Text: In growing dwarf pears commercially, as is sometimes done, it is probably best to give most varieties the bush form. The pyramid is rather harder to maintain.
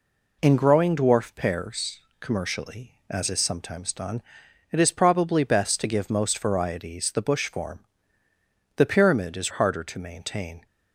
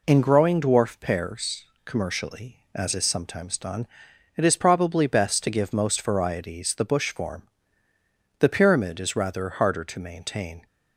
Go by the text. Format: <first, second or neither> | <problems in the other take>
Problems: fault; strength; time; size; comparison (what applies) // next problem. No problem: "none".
second | pauses between "pears" and "commercially"; slight; at 1.9 s; 0.22 s long; slight in the second // skips "rather"; at 9.5 s